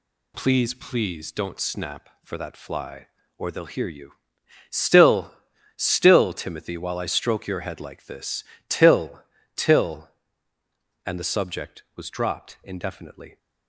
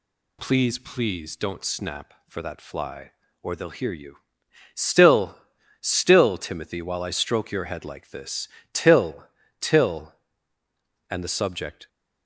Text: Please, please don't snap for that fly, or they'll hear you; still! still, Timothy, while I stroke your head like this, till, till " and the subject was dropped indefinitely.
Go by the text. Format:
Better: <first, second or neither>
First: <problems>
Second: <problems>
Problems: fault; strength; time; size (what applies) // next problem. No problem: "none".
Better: first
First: none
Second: stops before "was dropped indefinitely"; at 11.8 s